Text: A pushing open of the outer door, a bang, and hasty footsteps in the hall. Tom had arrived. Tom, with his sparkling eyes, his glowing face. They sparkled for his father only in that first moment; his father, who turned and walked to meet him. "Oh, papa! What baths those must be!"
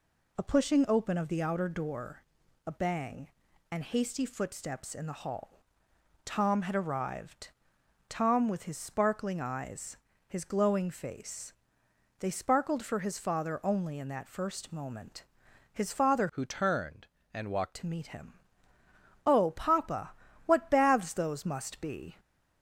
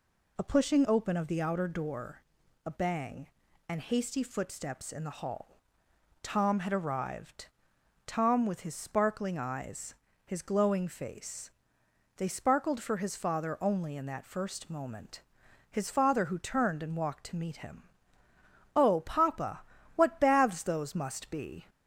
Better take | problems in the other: second | changes voice from "who" to "walked"; from 16.2 to 17.7 s; 1.5 s long

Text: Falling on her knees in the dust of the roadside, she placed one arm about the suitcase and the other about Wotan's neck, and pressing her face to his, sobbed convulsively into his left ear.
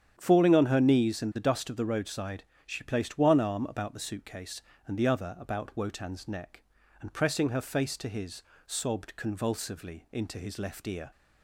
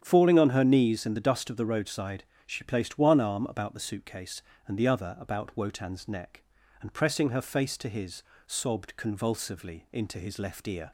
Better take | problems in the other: neither | starts louder than the rest; strong; the same in both

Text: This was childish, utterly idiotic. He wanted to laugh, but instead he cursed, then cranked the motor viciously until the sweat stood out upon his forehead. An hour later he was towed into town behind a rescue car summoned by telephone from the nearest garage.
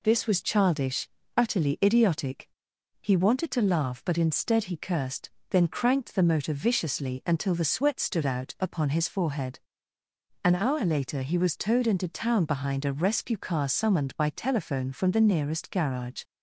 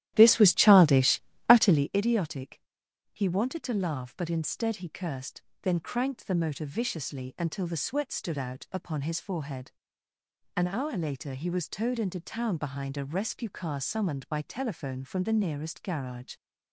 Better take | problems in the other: first | starts louder than the rest; strong; until 1.9 s; 13 dB

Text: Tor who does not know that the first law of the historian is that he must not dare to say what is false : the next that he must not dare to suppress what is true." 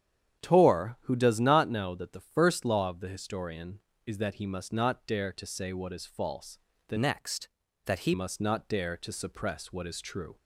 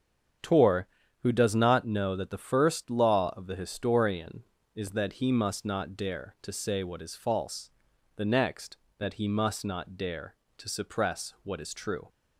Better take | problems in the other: second | starts louder than the rest; strong; until 1.4 s; 9 dB; strong in the second // changes voice from "next" to "he"; from 6.9 to 8.1 s; 1.2 s long

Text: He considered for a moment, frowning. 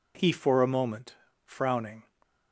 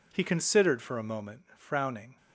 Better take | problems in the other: second | skips "considered"; at 0.3 s

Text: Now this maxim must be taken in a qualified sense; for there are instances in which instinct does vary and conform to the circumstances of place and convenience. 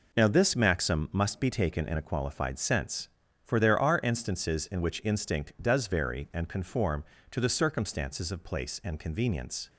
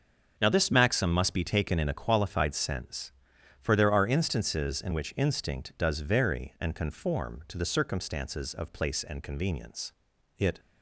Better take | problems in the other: first | starts louder than the rest; until 1.4 s; 6.5 dB // goes on to say "It"; slight; from 10.3 s on; 0.22 s long

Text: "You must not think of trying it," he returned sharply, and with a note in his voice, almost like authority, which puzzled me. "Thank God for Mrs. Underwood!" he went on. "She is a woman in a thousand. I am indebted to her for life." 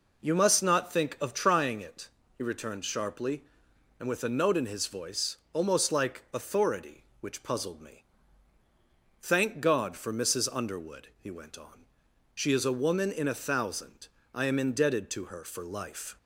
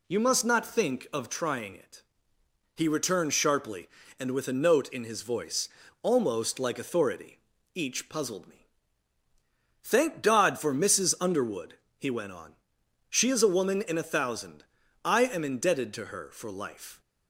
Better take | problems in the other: first | says "each" for "which"; at 7.7 s

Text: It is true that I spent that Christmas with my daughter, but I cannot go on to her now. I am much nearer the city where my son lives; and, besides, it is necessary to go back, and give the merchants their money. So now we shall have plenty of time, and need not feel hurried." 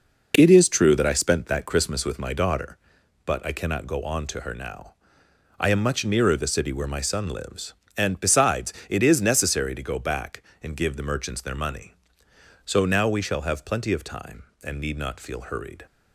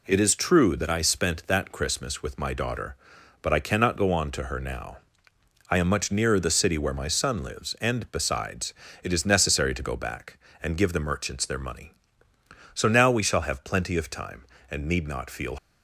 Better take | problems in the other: first | stops before "hurried"; at 15.5 s

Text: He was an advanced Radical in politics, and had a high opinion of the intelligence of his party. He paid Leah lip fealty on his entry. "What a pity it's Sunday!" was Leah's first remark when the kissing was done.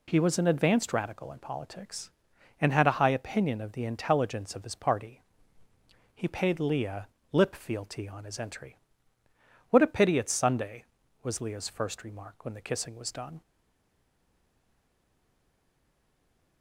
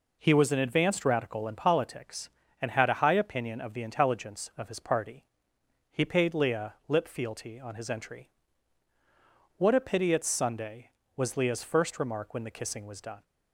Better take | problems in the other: second | pauses between "Leah" and "lip"; slight; at 7.0 s; 0.24 s long // stays silent after the last word; strong; from 13.4 s on; 3.2 s long

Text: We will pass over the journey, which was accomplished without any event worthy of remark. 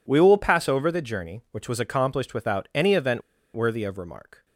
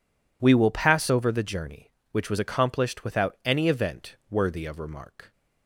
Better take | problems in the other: second | pauses between "event" and "worthy"; slight; at 3.2 s; 0.35 s long

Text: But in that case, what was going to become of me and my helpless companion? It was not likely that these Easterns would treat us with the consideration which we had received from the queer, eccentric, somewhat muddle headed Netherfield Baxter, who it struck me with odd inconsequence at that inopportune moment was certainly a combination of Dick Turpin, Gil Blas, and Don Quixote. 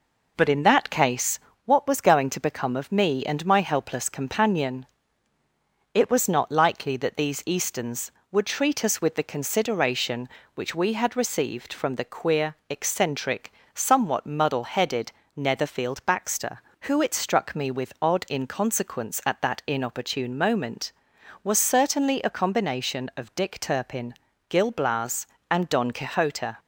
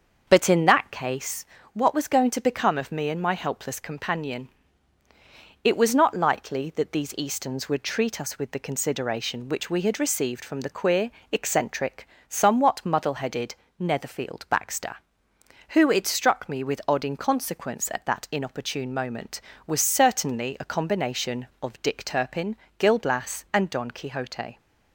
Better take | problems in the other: first | starts louder than the rest; until 1.4 s; 6.5 dB // pauses between "headed" and "Netherfield"; slight; at 13.5 s; 0.24 s long; slight in the first

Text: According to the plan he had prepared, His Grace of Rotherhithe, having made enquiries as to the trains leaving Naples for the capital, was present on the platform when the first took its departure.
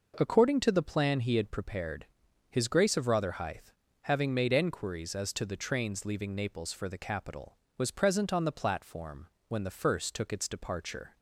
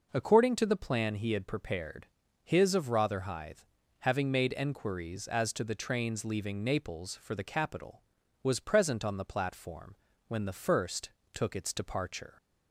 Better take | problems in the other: first | skips "Grace"; at 2.7 s // pauses between "platform" and "when"; slight; at 9.9 s; 0.30 s long; slight in the first // pauses between "first" and "took"; slight; at 11.1 s; 0.24 s long

